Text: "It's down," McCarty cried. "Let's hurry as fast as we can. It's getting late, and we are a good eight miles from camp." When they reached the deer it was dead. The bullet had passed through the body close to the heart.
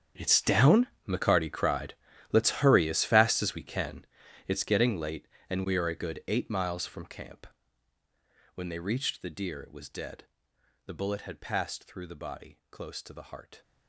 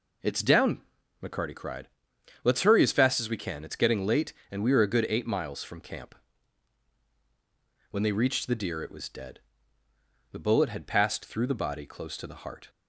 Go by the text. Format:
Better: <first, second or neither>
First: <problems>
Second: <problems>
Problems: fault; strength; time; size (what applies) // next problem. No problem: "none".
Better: second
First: gets quieter; strong; throughout; 17.5 dB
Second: none